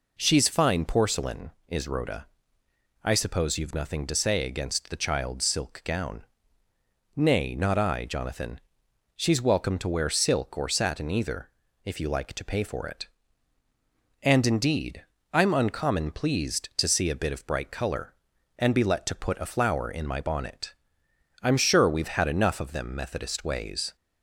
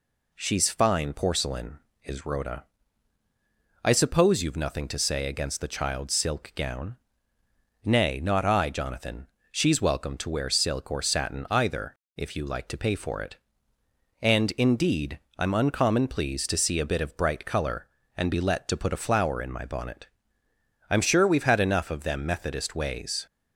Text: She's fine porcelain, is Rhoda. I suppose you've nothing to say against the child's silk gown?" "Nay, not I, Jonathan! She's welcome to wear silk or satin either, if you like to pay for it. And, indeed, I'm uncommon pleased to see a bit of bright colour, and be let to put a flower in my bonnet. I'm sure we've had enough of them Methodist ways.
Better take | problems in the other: neither | none

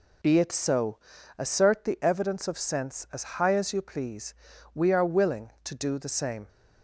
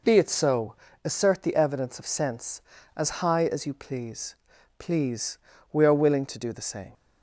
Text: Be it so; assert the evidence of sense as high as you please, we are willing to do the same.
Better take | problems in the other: first | says "please" twice; at 4.7 s

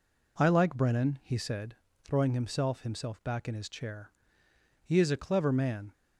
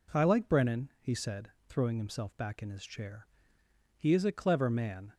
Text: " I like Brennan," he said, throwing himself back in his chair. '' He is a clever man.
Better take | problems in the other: second | says "himself" twice; at 2.8 s

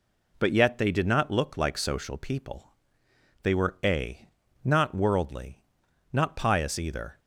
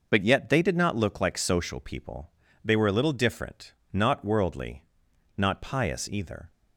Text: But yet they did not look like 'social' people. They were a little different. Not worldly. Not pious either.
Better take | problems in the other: second | skips "little different"; at 4.4 s

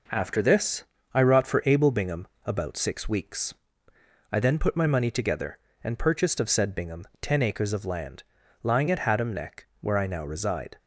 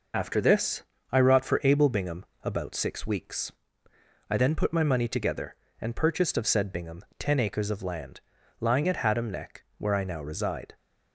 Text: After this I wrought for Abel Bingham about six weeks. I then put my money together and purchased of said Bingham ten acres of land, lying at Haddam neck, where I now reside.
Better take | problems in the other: first | loses the start of "After"; at 0.1 s; 80 ms // pauses between "this" and "I"; slight; at 0.8 s; 0.27 s long; slight in the first // pauses between "Bingham" and "about"; slight; at 2.2 s; 0.18 s long; slight in the first

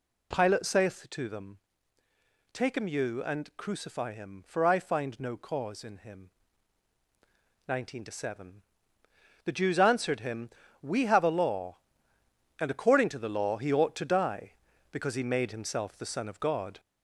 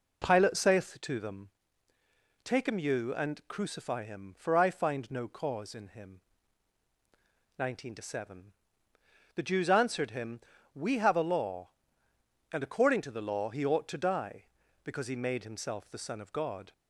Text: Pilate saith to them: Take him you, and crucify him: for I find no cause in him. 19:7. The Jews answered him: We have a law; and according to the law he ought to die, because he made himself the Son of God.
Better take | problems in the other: second | gets louder; slight; throughout; 3 dB

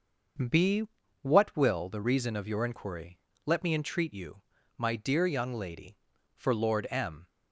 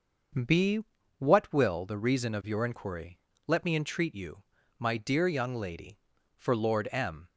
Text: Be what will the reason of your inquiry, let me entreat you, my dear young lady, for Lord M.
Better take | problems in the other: neither | starts louder than the rest; noticeable; the same in both // pauses between "Be" and "what"; slight; the same in both

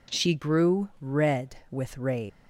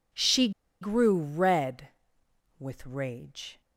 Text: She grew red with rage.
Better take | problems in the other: first | pauses between "She" and "grew"; slight; at 0.4 s; 0.31 s long

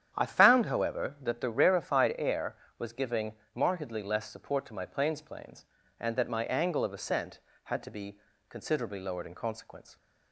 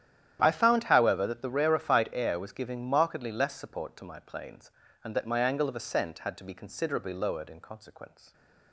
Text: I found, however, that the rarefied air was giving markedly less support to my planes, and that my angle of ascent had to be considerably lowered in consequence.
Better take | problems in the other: second | starts louder than the rest; strong; until 1.1 s; 9.5 dB; strong in the second // pauses between "giving" and "markedly"; slight; at 3.3 s; 0.22 s long // says "planes" twice; at 5.2 s // pauses between "be" and "considerably"; slight; at 8.1 s; 0.30 s long

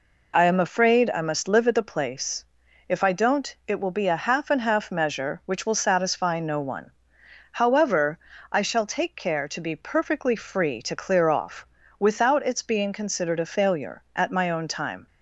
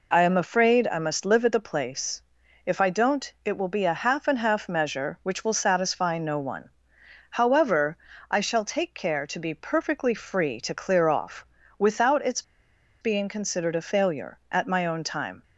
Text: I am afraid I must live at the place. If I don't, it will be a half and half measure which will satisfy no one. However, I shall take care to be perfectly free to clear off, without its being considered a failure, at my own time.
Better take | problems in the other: first | pauses between "its" and "being"; noticeable; at 12.4 s; 0.59 s long

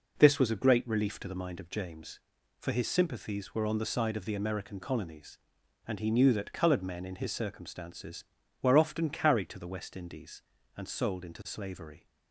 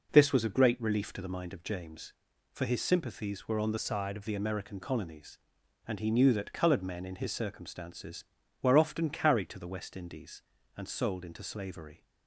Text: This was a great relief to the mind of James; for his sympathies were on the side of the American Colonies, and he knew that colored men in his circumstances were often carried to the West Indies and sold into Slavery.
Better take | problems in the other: first | changes voice from "side" to "of"; from 3.7 to 4.2 s; 0.5 s long

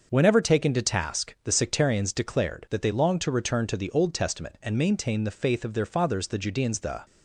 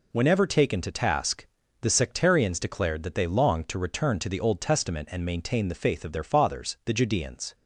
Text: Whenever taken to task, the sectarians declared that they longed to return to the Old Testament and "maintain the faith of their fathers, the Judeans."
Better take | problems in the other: second | starts louder than the rest; until 1.1 s; 6.5 dB // goes on to say "The"; slight; from 6.8 s on; 0.24 s long

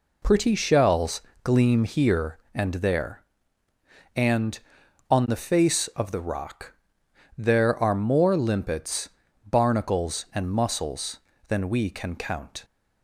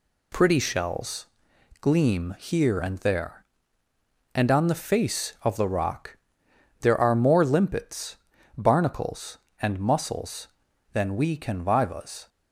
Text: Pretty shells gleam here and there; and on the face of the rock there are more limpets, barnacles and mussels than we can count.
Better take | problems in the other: first | pauses between "shells" and "gleam"; noticeable; at 1.2 s; 0.54 s long; slight in the first // pauses between "rock" and "there"; noticeable; at 6.1 s; 0.64 s long; noticeable in the first // says "vivas" for "count"; at 11.6 s

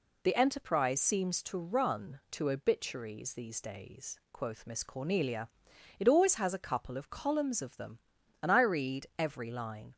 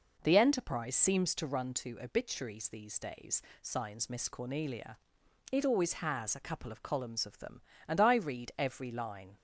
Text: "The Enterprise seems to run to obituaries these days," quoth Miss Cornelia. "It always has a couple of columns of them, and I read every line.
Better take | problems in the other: first | says "signs" for "quoth"; at 3.6 s

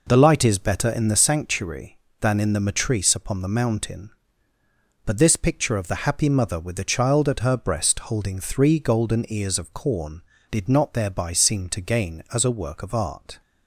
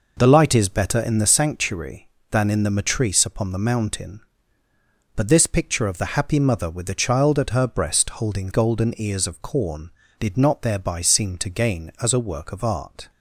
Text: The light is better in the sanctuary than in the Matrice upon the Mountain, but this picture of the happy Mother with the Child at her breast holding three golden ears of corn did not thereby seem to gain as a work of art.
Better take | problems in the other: first | skips "three"; at 8.5 s

